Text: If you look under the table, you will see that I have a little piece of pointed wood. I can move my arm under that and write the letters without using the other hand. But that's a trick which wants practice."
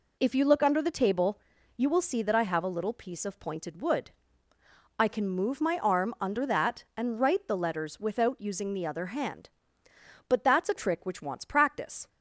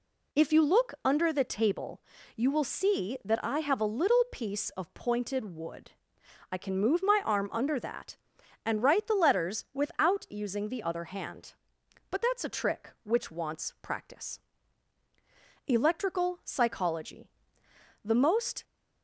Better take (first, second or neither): first